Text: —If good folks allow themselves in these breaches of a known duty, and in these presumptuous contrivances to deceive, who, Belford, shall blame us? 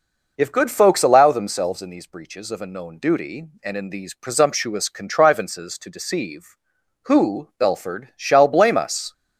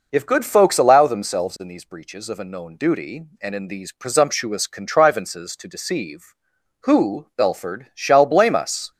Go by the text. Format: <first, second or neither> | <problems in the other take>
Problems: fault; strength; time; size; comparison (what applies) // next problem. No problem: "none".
neither | none